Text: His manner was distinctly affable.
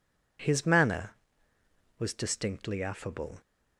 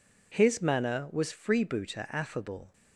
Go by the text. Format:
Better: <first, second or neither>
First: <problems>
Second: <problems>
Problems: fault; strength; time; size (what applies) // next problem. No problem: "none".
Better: first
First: none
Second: says "freebooter" for "distinctly"; at 1.3 s